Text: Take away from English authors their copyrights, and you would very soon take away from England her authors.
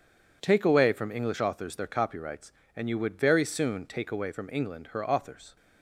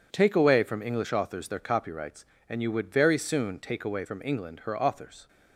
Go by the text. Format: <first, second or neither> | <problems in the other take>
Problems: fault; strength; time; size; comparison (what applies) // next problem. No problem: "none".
neither | none